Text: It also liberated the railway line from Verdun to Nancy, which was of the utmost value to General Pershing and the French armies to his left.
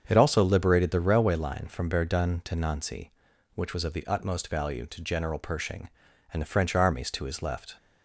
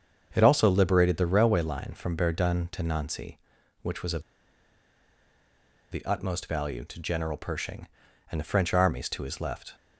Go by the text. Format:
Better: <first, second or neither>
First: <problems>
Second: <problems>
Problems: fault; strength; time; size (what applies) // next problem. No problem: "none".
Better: first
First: starts louder than the rest; until 1.0 s; 7 dB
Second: starts louder than the rest; until 1.3 s; 7 dB // pauses between "of" and "the"; strong; at 4.2 s; 1.6 s long